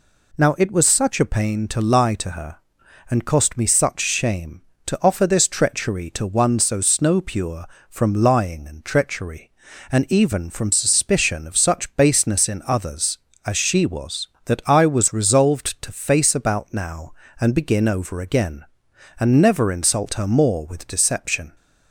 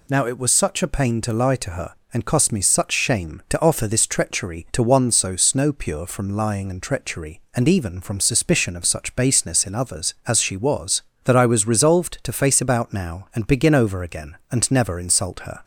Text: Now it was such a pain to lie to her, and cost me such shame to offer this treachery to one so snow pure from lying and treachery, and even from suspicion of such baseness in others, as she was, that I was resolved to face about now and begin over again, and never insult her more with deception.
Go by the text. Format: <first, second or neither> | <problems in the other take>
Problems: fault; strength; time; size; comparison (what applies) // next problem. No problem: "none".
first | stops before "more with deception"; at 15.6 s